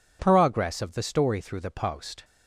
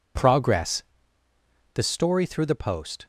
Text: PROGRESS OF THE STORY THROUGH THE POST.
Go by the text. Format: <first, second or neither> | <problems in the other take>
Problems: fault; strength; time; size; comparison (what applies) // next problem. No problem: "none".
first | skips "OF"; at 1.2 s